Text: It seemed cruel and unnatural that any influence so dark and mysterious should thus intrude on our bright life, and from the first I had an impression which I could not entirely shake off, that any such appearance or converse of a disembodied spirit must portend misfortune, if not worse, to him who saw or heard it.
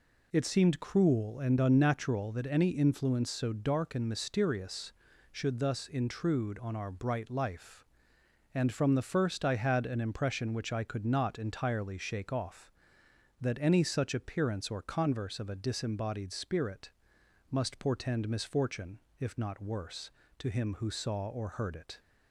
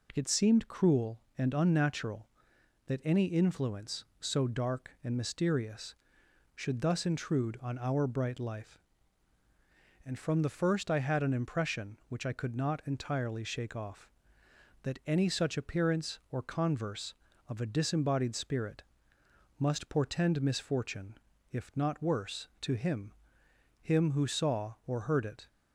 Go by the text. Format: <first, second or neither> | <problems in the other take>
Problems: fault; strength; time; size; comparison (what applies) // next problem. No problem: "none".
first | pauses between "spirit" and "must"; noticeable; at 18.8 s; 0.76 s long; noticeable in the first // says "him" twice; at 23.7 s